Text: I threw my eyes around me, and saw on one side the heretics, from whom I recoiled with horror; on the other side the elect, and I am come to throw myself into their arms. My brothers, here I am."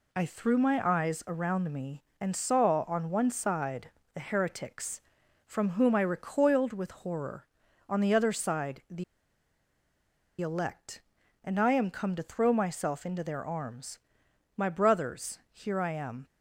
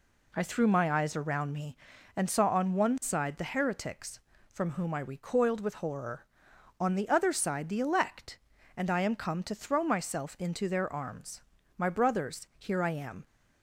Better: second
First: pauses between "side" and "the"; slight; at 3.9 s; 0.22 s long // pauses between "the" and "elect"; strong; at 9.0 s; 1.3 s long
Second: none

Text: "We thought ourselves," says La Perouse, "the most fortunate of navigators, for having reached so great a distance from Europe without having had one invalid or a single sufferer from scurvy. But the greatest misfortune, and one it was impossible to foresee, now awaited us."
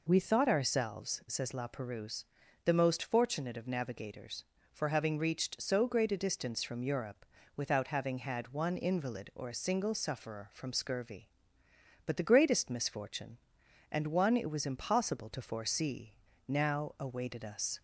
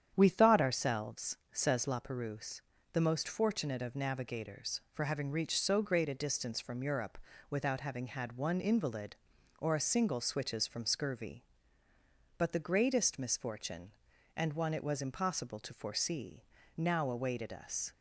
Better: first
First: pauses between "Europe" and "without"; slight; at 7.2 s; 0.32 s long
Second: starts louder than the rest; strong; until 1.1 s; 9 dB // pauses between "Europe" and "without"; slight; at 7.1 s; 0.32 s long // says "switches" for "sufferer"; at 10.2 s

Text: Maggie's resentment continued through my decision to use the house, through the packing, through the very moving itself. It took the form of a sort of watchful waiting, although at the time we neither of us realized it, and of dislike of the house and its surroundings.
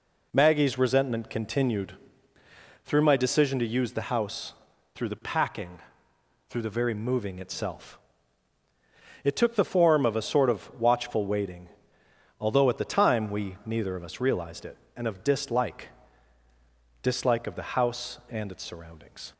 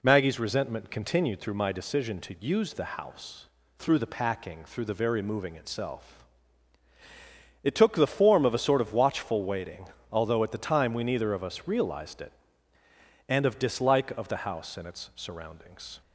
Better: second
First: pauses between "continued" and "through"; noticeable; at 1.9 s; 0.90 s long // says "dislike" twice; at 17.0 s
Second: none

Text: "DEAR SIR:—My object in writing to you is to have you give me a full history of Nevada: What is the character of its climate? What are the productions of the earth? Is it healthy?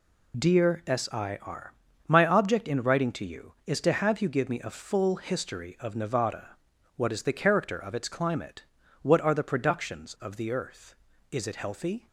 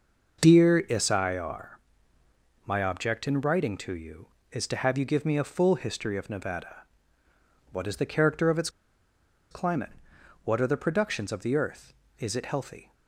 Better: first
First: none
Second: pauses between "its" and "climate"; noticeable; at 8.6 s; 0.81 s long

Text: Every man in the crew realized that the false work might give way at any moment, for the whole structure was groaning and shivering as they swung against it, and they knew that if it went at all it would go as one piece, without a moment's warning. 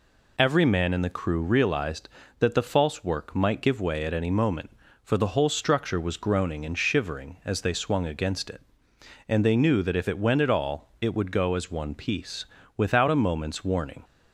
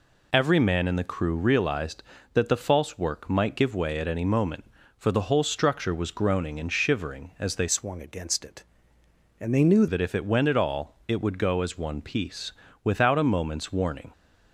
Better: first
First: none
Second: changes voice from "swung" to "knew"; from 7.6 to 9.8 s; 2.2 s long

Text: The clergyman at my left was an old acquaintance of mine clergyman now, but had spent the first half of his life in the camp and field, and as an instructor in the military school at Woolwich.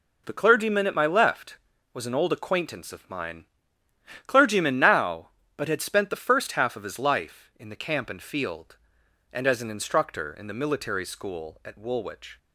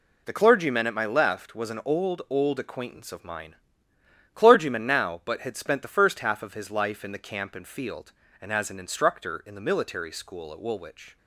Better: first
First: pauses between "mine" and "clergyman"; noticeable; at 3.4 s; 0.80 s long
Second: says "old" twice; at 2.2 s // pauses between "mine" and "clergyman"; noticeable; at 3.5 s; 0.80 s long

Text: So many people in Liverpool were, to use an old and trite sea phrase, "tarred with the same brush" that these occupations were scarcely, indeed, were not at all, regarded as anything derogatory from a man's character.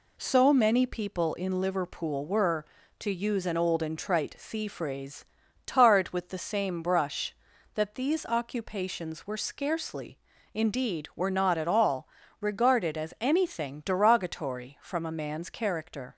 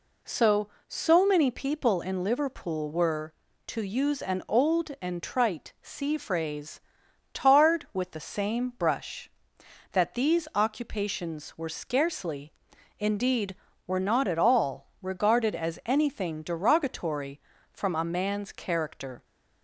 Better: first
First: none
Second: says "So" twice; at 0.8 s

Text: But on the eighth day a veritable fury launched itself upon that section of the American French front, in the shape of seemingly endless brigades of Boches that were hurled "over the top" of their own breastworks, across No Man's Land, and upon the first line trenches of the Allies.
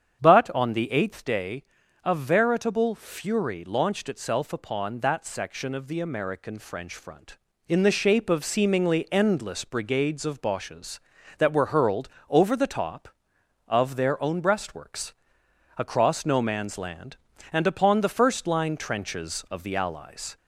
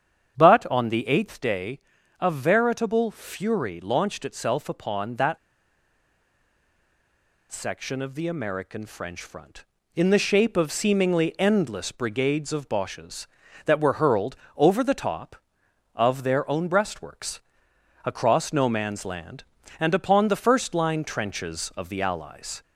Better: first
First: starts louder than the rest; strong; until 1.2 s; 8 dB // pauses between "day" and "a"; at 1.6 s; 0.42 s long // pauses between "hurled" and "over"; slight; at 12.0 s; 0.20 s long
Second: starts louder than the rest; strong; until 1.4 s; 8 dB // pauses between "day" and "a"; at 1.7 s; 0.42 s long // pauses between "that" and "section"; strong; at 5.3 s; 2.1 s long // pauses between "hurled" and "over"; slight; at 14.3 s; 0.20 s long

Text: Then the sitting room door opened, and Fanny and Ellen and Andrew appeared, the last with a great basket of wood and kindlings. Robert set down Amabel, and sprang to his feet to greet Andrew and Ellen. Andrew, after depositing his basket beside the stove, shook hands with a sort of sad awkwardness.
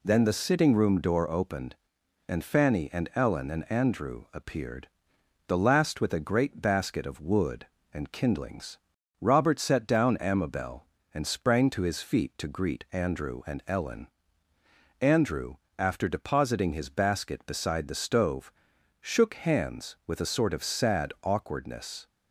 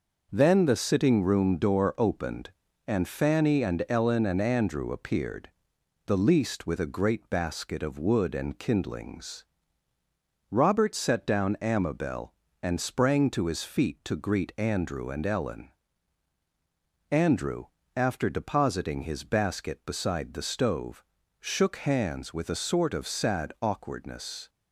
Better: first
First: none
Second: says "least" for "last"; at 6.1 s

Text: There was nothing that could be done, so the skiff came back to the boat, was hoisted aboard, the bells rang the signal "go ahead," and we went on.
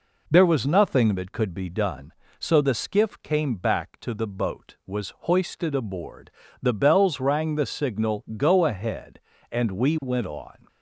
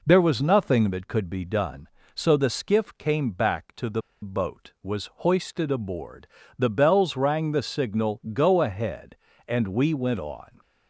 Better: first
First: none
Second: pauses between "the" and "boat"; slight; at 4.0 s; 0.21 s long

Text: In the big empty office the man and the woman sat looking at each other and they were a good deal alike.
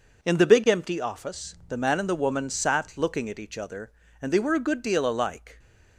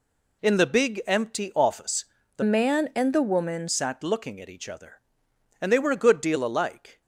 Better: first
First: none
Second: pauses between "office" and "the"; slight; at 2.0 s; 0.32 s long // changes voice from "man" to "woman"; from 2.4 to 3.6 s; 1.2 s long

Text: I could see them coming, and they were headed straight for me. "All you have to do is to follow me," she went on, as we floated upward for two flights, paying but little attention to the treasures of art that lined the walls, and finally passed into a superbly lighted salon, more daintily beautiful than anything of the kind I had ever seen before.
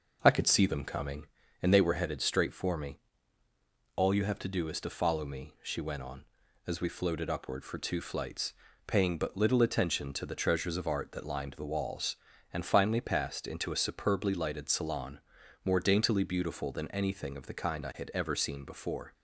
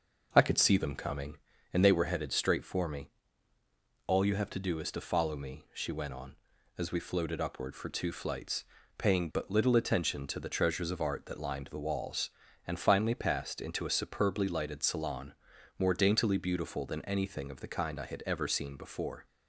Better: neither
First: none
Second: none

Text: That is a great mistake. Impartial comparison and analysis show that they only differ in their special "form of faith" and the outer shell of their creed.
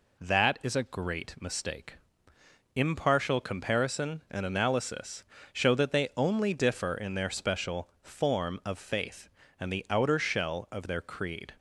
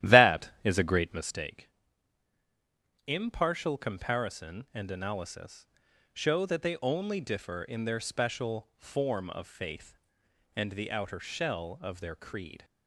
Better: first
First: pauses between "analysis" and "show"; slight; at 5.2 s; 0.28 s long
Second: starts louder than the rest; strong; until 1.4 s; 13 dB // pauses between "analysis" and "show"; noticeable; at 5.6 s; 0.46 s long

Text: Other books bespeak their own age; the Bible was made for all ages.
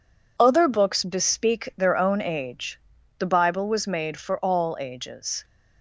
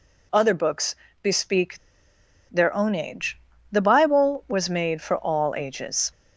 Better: first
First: none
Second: pauses between "books" and "bespeak"; slight; at 0.9 s; 0.28 s long // pauses between "bespeak" and "their"; noticeable; at 1.7 s; 0.71 s long

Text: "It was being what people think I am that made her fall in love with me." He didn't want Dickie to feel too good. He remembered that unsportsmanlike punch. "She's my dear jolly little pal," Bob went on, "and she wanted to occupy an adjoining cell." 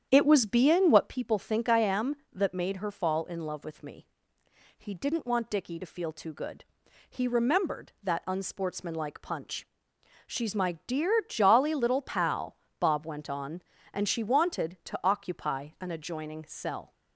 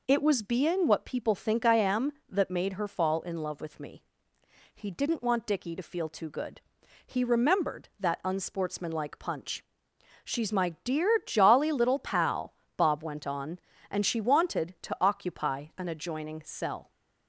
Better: second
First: starts louder than the rest; strong; until 1.2 s; 9 dB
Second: none

